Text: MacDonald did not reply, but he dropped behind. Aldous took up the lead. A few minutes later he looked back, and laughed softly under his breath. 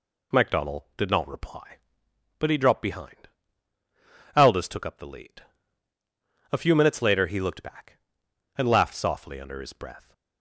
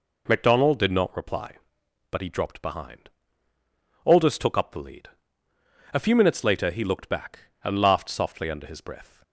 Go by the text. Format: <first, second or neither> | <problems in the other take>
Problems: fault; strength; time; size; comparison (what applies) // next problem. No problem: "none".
neither | none